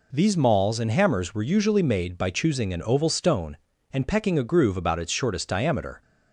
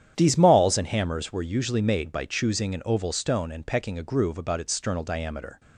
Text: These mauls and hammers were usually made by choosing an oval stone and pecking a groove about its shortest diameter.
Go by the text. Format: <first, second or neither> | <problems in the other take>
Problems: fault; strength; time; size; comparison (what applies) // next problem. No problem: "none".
first | starts louder than the rest; strong; until 1.1 s; 9.5 dB // says "sternal" for "shortest"; at 4.7 s